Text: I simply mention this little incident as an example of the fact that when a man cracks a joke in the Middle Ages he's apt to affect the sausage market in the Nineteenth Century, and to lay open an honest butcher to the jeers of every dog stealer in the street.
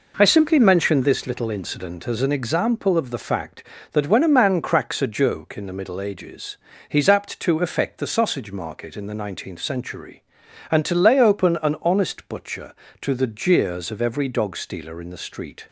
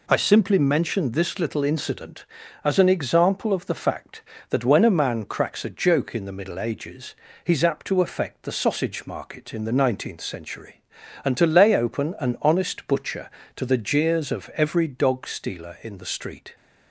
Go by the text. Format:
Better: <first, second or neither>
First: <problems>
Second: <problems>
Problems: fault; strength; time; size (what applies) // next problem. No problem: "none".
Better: neither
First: pauses between "Ages" and "he's"; slight; at 6.5 s; 0.32 s long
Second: pauses between "Ages" and "he's"; slight; at 7.1 s; 0.30 s long